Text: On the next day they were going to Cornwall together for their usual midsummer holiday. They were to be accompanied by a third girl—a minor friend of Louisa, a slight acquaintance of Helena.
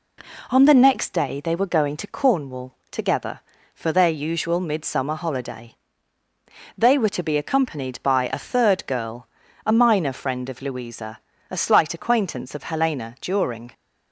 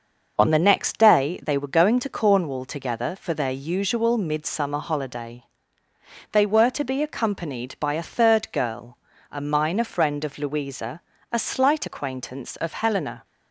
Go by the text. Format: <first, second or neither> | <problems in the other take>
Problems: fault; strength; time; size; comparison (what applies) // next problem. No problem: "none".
second | pauses between "Cornwall" and "together"; slight; at 2.7 s; 0.16 s long // goes on to say "During"; from 13.1 s on; 0.52 s long